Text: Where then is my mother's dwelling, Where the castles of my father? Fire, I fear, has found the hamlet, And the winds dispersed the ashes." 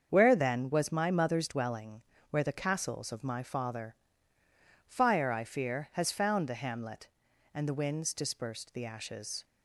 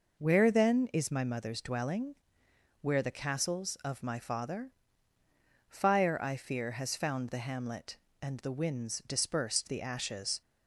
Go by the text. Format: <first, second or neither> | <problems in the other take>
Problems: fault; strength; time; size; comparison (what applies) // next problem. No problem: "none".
second | starts louder than the rest; until 1.1 s; 7 dB // says "was" for "is"; at 0.7 s